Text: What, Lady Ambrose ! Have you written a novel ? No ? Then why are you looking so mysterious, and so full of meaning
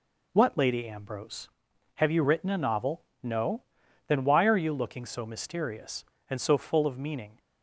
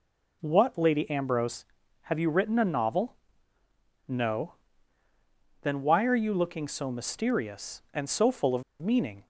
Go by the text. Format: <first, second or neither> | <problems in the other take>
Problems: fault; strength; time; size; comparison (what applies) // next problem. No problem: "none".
first | pauses between "of" and "meaning"; slight; at 8.6 s; 0.19 s long